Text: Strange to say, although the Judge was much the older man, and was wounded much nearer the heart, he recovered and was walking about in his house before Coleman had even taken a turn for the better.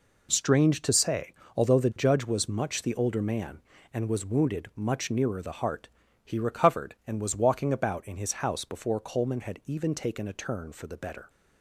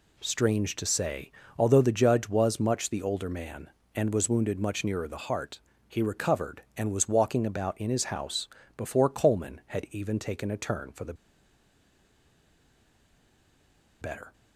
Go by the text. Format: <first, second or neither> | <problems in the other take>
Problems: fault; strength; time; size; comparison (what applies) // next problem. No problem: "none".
first | pauses between "house" and "before"; slight; at 8.4 s; 0.30 s long // pauses between "the" and "better"; strong; at 11.1 s; 2.8 s long